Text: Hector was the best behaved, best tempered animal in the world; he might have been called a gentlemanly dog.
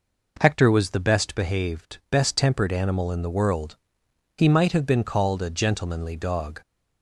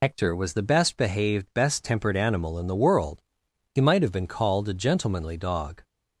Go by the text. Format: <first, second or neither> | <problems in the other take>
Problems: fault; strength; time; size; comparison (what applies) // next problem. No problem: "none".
first | loses the start of "Hector"; at 0.0 s; 50 ms